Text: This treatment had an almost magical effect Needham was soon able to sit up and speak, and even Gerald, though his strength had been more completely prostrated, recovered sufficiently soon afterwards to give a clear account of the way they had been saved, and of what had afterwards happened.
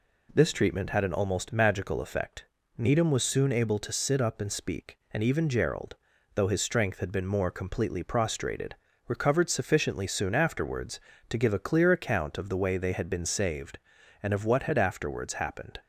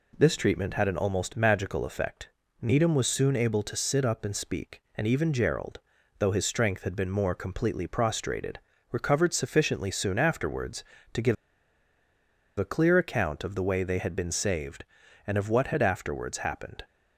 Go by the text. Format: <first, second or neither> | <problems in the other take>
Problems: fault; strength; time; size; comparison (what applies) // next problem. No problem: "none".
first | pauses between "effect" and "Needham"; slight; at 2.2 s; 0.34 s long; slight in the first // pauses between "give" and "a"; at 11.3 s; 1.2 s long